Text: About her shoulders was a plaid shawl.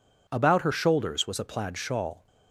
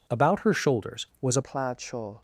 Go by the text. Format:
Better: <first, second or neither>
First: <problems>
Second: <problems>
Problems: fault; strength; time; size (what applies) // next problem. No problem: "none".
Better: first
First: none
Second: changes voice at "plaid"; from 1.4 s on; 0.8 s long